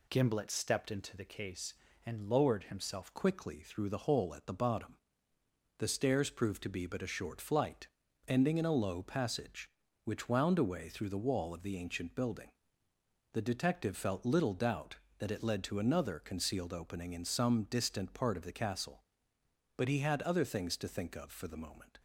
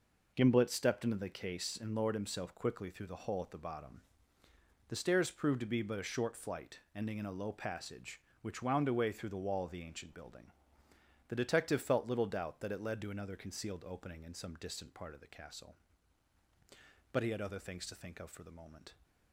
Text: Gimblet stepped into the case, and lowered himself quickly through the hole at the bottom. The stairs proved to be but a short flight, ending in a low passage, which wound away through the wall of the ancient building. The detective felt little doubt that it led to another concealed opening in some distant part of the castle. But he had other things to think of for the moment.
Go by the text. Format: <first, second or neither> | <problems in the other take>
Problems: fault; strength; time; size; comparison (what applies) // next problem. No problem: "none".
second | changes voice at "quickly"; from 3.1 s on; 18.8 s long